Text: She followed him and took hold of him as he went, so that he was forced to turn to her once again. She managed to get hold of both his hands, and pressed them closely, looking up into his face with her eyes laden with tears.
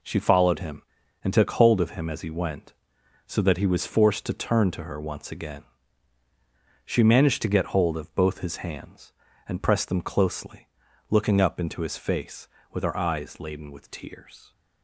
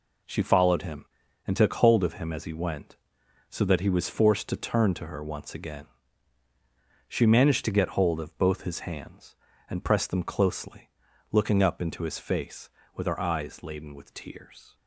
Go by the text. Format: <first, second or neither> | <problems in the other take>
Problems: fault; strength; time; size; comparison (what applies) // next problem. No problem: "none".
neither | none